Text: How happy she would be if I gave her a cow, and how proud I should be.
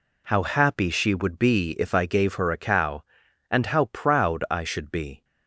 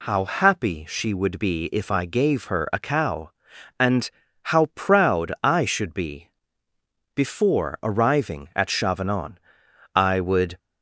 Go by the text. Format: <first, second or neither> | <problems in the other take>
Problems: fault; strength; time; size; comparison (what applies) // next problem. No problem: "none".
first | pauses between "and" and "how"; at 4.0 s; 0.40 s long // goes on to say "Before arriving at Chavanon I would"; strong; from 7.1 s on; 3.4 s long